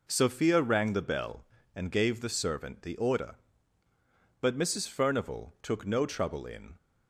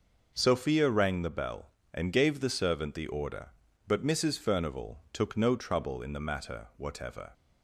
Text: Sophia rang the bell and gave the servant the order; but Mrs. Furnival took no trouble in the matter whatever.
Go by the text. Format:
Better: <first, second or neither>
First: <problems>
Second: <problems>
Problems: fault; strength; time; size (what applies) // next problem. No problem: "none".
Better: second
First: stops before "the matter whatever"; at 6.7 s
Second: none